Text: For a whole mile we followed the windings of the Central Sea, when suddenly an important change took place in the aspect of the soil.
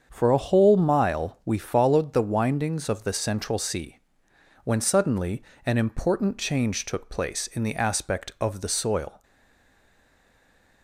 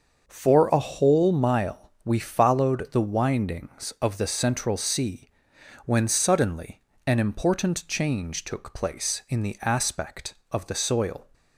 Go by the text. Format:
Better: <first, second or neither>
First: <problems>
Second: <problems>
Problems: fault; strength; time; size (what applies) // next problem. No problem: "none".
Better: second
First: starts louder than the rest; strong; until 1.1 s; 7 dB // pauses between "suddenly" and "an"; slight; at 5.4 s; 0.22 s long // stays silent after the last word; noticeable; from 9.2 s on; 1.6 s long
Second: starts louder than the rest; until 1.2 s; 6.5 dB // pauses between "suddenly" and "an"; slight; at 6.8 s; 0.24 s long